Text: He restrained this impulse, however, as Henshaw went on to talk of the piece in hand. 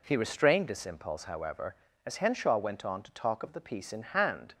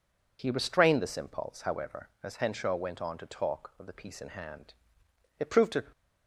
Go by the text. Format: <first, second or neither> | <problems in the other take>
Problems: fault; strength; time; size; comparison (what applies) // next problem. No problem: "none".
first | goes on to say "It proved to"; slight; from 5.3 s on; 0.46 s long